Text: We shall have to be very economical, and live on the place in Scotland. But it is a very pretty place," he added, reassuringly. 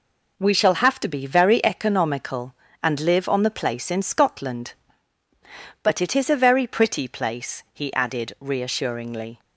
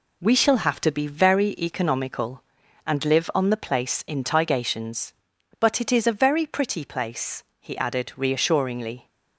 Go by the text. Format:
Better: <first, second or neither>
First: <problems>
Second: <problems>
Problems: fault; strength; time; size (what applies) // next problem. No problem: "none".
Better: first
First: none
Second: says "Tigations" for "Scotland"; at 4.2 s